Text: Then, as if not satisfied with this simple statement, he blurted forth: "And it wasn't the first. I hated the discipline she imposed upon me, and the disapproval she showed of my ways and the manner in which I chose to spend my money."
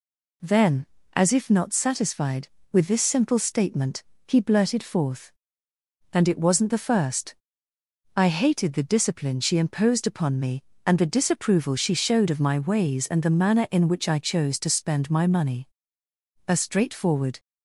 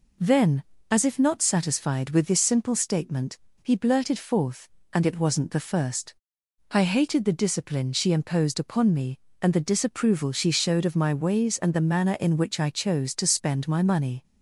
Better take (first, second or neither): second